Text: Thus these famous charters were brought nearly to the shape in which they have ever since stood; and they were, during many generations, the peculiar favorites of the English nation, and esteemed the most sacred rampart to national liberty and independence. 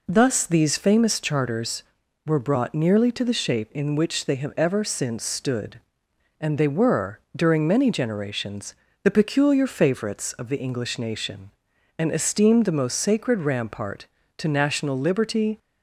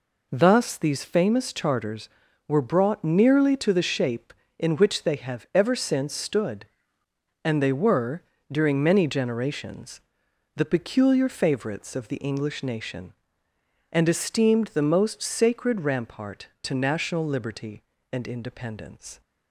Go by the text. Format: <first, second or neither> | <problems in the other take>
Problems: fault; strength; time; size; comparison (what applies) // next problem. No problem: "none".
second | stops before "and independence"; at 15.5 s